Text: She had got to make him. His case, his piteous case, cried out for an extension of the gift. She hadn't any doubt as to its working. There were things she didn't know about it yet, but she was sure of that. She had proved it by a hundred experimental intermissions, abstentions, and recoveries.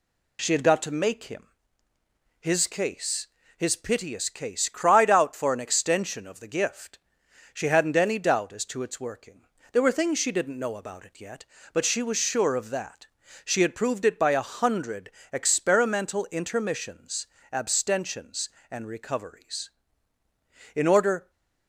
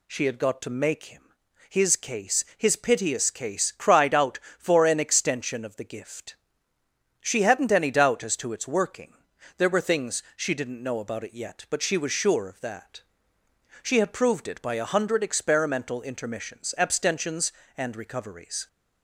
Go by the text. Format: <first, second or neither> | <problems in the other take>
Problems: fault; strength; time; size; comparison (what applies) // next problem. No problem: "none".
second | pauses between "hundred" and "experimental"; slight; at 15.1 s; 0.20 s long // goes on to say "In order"; from 20.7 s on; 0.56 s long